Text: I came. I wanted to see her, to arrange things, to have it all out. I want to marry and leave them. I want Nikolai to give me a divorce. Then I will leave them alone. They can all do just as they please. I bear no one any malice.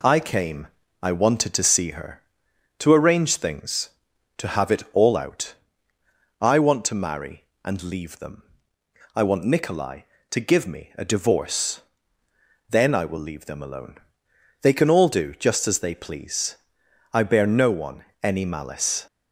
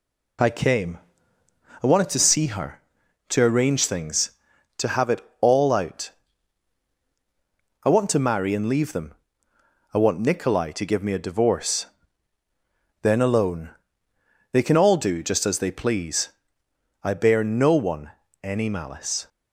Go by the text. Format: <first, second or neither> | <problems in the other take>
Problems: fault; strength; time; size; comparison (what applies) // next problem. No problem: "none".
first | pauses between "it" and "all"; slight; at 5.1 s; 0.22 s long // skips "I will leave them"; at 13.2 s // pauses between "one" and "any"; slight; at 18.1 s; 0.28 s long; slight in the first